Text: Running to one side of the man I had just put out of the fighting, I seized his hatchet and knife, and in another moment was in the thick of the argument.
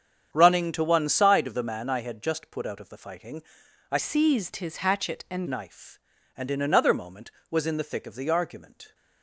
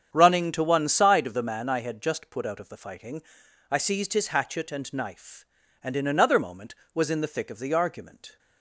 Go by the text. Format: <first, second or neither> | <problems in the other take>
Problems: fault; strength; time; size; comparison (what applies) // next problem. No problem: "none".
second | starts louder than the rest; strong; until 1.3 s; 8 dB; strong in the second // changes voice from "seized" to "and"; from 3.9 to 5.4 s; 1.5 s long